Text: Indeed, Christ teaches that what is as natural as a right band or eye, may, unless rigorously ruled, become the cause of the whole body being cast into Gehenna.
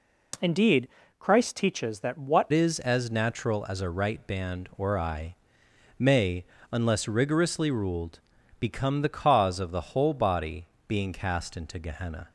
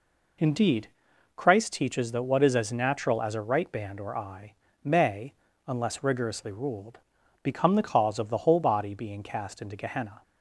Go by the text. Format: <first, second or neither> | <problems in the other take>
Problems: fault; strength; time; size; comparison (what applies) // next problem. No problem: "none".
second | changes voice at "is"; from 2.5 s on; 9.8 s long // pauses between "body" and "being"; slight; at 10.6 s; 0.22 s long